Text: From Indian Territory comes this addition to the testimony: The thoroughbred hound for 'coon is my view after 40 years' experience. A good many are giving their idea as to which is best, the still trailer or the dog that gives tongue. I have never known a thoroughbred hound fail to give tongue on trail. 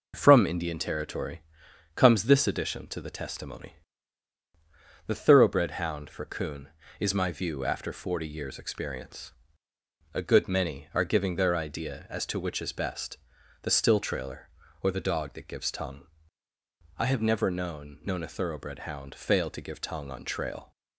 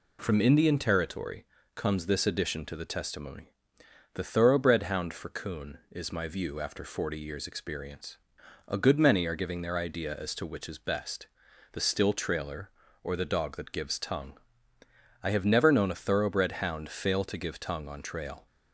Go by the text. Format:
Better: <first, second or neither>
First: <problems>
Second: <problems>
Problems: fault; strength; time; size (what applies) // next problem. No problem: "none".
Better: second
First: pauses between "Territory" and "comes"; noticeable; at 1.4 s; 0.56 s long // says "known" twice; at 18.0 s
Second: pauses between "Territory" and "comes"; slight; at 1.4 s; 0.30 s long